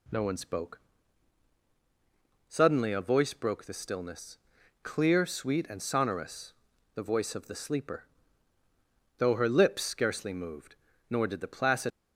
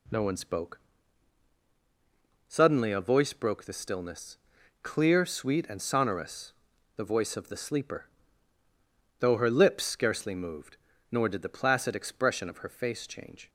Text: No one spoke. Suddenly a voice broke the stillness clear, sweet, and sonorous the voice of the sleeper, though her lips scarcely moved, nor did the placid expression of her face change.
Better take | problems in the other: second | pauses between "stillness" and "clear"; noticeable; at 4.3 s; 0.46 s long; noticeable in the second // pauses between "sonorous" and "the"; at 6.5 s; 0.40 s long; also in the second // stops before "expression of her face change"; at 11.9 s

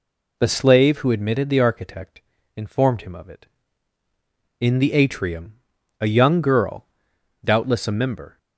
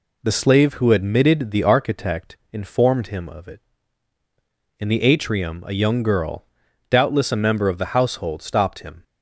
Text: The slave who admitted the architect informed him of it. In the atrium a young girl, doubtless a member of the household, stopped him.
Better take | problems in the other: second | pauses between "architect" and "informed"; slight; at 2.2 s; 0.34 s long; slight in the second // pauses between "atrium" and "a"; noticeable; at 5.5 s; 0.46 s long // stops before "of the household stopped him"; at 8.3 s

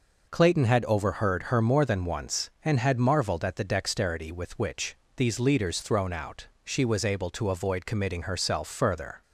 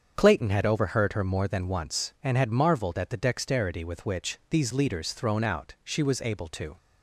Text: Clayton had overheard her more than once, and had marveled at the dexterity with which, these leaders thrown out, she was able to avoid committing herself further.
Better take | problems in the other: first | starts louder than the rest; until 1.1 s; 7 dB // stops before "avoid committing herself further"; at 6.7 s

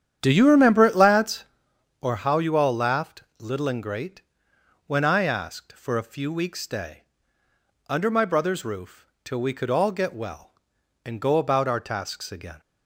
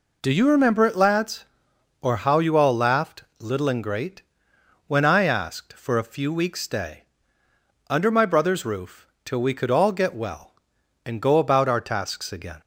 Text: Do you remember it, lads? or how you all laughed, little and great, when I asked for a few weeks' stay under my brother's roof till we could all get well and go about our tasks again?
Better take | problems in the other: second | starts louder than the rest; strong; until 1.6 s; 9.5 dB // pauses between "stay" and "under"; noticeable; at 7.0 s; 0.86 s long; noticeable in the second // pauses between "roof" and "till"; slight; at 9.0 s; 0.18 s long; slight in the second

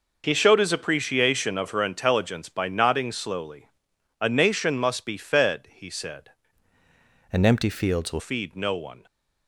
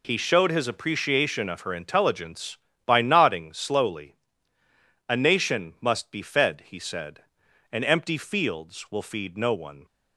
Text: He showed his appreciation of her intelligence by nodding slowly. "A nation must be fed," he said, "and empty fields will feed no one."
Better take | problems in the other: second | changes voice from "and" to "will"; from 7.3 to 8.1 s; 0.8 s long

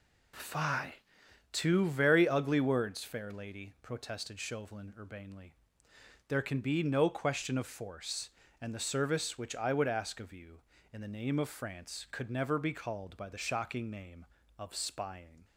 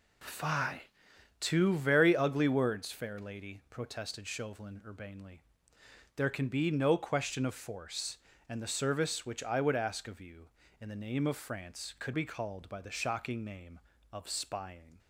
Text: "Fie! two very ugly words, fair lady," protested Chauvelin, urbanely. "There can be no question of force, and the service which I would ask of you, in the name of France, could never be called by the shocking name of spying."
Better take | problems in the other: first | skips "never"; at 12.1 s

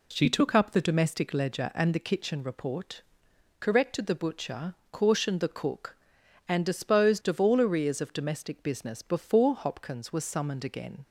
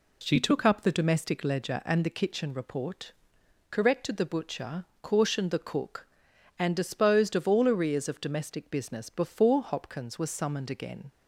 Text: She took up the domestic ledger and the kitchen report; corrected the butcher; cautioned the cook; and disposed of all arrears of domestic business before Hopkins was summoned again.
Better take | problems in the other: neither | none

